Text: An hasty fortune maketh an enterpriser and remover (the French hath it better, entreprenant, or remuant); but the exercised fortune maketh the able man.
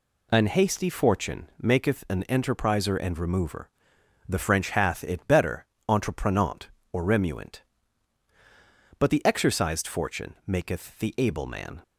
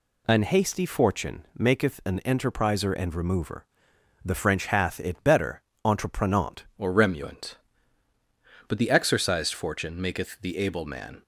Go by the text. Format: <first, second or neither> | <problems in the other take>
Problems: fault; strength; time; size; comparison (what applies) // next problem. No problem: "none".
first | changes voice at "or"; from 6.7 s on; 4.5 s long